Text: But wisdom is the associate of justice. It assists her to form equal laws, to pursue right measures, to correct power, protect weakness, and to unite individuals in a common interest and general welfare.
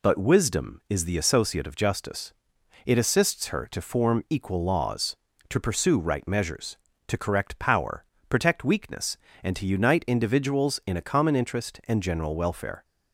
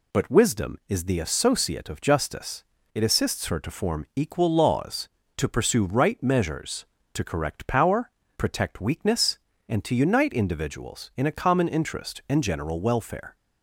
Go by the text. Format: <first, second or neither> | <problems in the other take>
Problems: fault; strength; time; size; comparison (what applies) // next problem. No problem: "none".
neither | none